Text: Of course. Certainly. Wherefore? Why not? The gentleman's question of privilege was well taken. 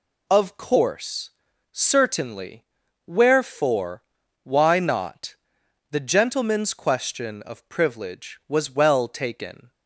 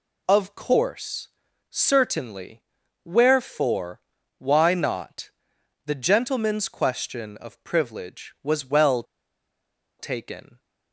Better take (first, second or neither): first